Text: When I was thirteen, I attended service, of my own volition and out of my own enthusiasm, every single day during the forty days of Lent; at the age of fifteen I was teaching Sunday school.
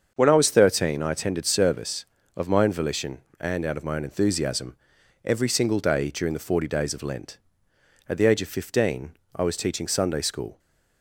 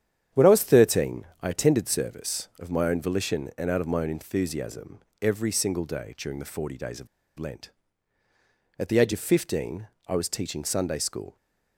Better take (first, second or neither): first